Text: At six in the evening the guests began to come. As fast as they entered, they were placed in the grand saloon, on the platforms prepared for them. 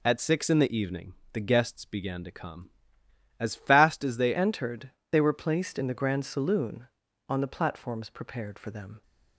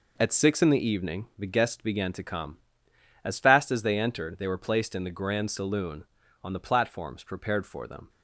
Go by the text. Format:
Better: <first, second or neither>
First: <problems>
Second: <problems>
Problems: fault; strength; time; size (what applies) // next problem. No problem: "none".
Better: second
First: pauses between "evening" and "the"; slight; at 1.1 s; 0.20 s long // changes voice at "entered"; from 4.3 s on; 4.7 s long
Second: none